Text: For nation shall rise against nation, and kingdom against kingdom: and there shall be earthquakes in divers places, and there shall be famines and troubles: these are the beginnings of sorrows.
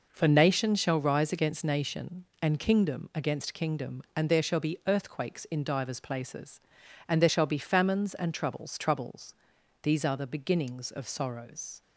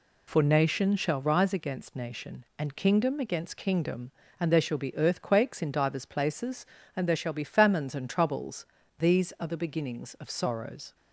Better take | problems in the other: second | says "troubles" twice; at 8.7 s

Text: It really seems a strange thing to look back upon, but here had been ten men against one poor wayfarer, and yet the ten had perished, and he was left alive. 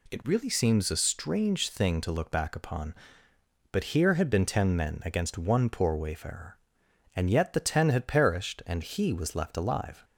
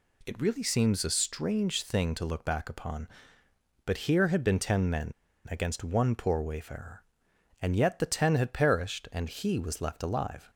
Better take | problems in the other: first | pauses between "men" and "against"; at 5.1 s; 0.37 s long

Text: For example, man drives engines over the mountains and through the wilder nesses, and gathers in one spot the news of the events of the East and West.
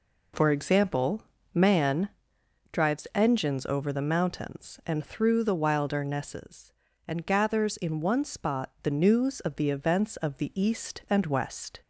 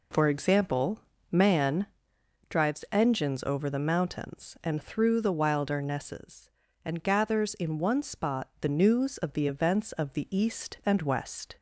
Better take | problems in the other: neither | pauses between "man" and "drives"; noticeable; the same in both

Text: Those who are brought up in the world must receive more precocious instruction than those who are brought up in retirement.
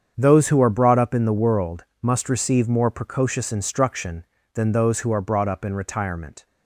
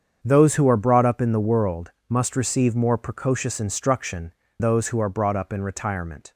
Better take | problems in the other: first | starts louder than the rest; strong; until 1.2 s; 7.5 dB; strong in the first // pauses between "world" and "must"; slight; at 1.8 s; 0.18 s long; slight in the first // skips "than"; at 4.4 s

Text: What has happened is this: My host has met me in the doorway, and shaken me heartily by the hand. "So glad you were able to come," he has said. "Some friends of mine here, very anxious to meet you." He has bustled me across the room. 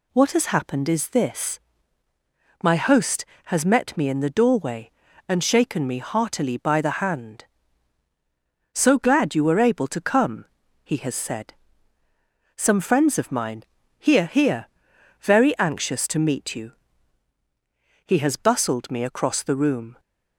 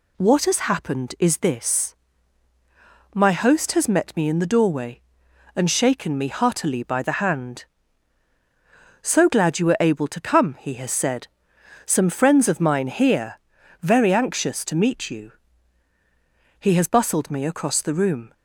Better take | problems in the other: second | pauses between "mine" and "here"; at 13.6 s; 0.38 s long // says "here" twice; at 14.2 s

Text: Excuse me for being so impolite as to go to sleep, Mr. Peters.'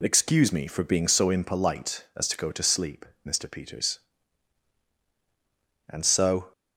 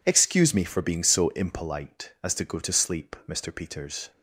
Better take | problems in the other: second | goes on to say "And so"; noticeable; from 5.8 s on; 0.64 s long

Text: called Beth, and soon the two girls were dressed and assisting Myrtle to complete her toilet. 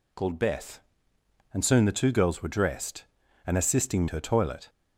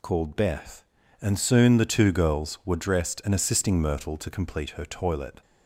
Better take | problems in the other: second | skips "Myrtle to complete"; at 4.0 s

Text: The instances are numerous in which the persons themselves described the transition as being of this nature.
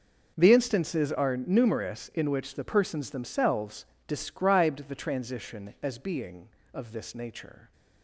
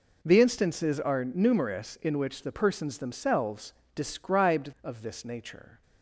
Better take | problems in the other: first | pauses between "themselves" and "described"; slight; at 3.7 s; 0.22 s long; slight in the first // skips "the transition as being"; at 4.7 s

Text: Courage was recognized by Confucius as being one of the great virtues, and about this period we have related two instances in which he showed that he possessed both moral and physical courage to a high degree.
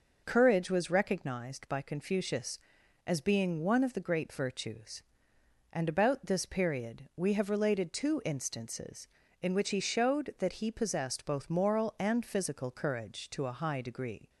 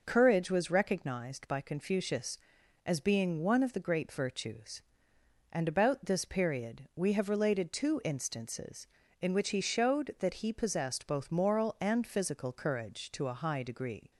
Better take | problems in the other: neither | none

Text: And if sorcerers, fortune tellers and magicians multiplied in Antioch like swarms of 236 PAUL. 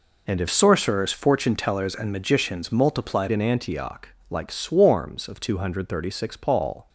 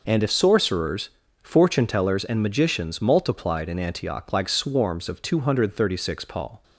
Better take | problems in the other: second | changes voice from "sorcerers" to "multiplied"; from 0.5 to 3.2 s; 2.7 s long // pauses between "Antioch" and "like"; slight; at 4.0 s; 0.22 s long

